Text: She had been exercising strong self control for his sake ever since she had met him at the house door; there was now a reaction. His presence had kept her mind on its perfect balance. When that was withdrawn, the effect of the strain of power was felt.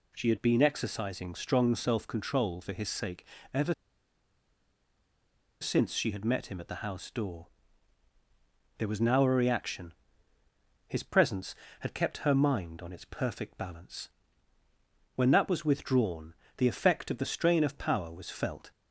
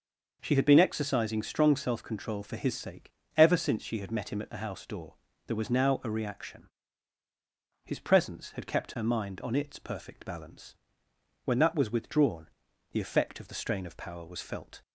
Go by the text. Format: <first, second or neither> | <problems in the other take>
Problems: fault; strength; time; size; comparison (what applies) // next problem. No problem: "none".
second | pauses between "sake" and "ever"; slight; at 3.2 s; 0.26 s long; slight in the second // pauses between "ever" and "since"; strong; at 3.7 s; 1.8 s long